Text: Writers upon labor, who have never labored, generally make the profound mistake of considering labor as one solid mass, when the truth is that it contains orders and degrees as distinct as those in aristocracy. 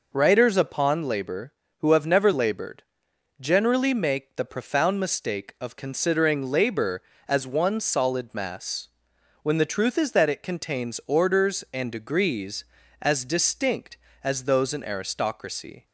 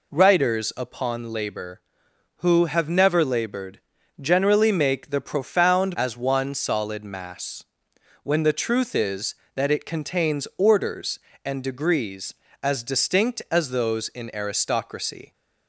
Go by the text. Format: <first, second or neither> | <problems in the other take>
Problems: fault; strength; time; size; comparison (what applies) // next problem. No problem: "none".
first | skips "mistake of considering labor"; at 5.9 s